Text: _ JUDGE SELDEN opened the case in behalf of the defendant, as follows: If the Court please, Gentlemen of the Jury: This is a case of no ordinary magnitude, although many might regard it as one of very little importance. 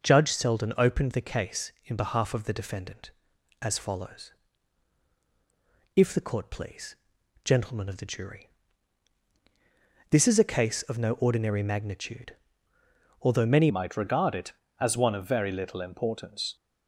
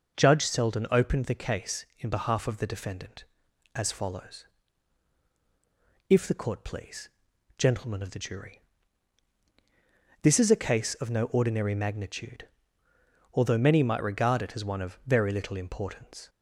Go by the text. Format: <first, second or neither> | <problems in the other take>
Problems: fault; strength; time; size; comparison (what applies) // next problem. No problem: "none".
second | changes voice at "might"; from 13.6 s on; 2.9 s long